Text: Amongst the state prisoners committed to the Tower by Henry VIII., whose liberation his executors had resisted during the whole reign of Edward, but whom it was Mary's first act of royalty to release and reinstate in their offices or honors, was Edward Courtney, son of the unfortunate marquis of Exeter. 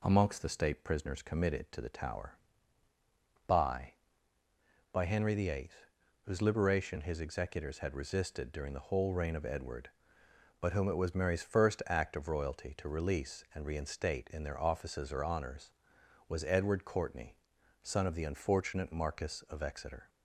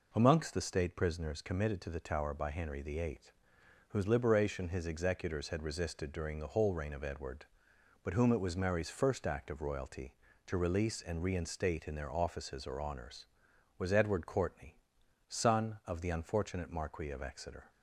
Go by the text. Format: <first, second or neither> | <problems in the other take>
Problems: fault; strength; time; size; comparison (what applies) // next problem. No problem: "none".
second | says "by" twice; at 4.9 s